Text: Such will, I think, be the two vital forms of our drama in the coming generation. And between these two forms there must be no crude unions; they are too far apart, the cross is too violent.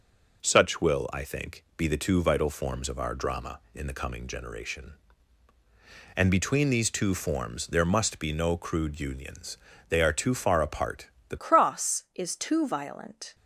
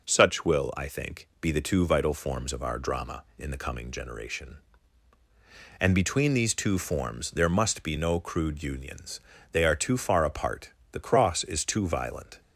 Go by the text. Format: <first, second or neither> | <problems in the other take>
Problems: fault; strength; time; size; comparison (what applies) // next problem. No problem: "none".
second | changes voice at "cross"; from 11.3 s on; 2.0 s long